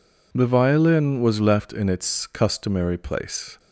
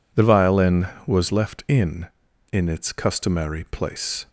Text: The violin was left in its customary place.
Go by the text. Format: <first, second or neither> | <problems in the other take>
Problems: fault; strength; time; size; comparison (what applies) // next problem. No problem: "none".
first | says "in" twice; at 2.5 s